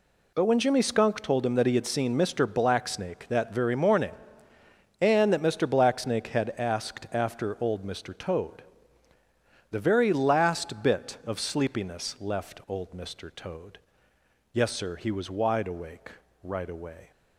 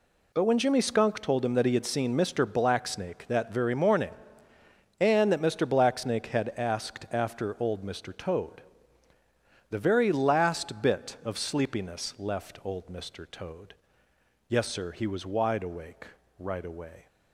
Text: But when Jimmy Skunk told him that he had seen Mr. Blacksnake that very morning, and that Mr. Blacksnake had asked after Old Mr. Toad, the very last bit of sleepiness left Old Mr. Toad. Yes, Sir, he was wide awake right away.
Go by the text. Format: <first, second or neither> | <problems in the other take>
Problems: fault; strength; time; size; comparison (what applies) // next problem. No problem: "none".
neither | pauses between "awake" and "right"; slight; the same in both